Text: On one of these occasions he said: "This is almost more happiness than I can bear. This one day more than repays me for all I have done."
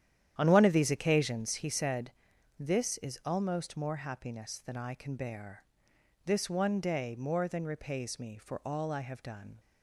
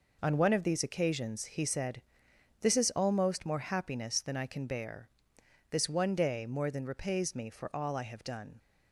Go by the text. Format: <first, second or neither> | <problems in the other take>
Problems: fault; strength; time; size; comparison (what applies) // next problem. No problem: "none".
second | starts louder than the rest; strong; until 1.9 s; 10.5 dB